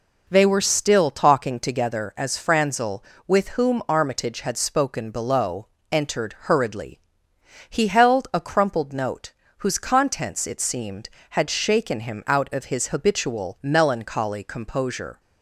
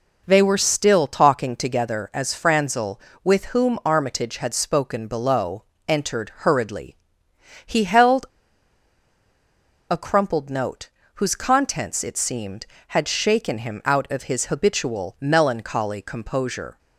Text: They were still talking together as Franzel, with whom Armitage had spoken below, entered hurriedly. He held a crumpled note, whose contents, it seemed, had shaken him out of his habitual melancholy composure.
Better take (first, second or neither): first